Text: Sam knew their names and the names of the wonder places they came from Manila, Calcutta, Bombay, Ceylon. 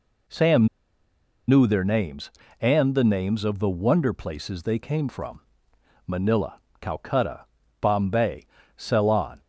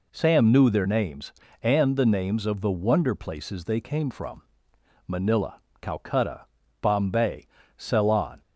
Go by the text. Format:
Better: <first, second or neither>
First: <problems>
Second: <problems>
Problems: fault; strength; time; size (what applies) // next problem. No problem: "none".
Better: second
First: pauses between "Sam" and "knew"; noticeable; at 0.6 s; 0.81 s long // pauses between "from" and "Manila"; noticeable; at 5.4 s; 0.66 s long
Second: pauses between "from" and "Manila"; noticeable; at 4.4 s; 0.64 s long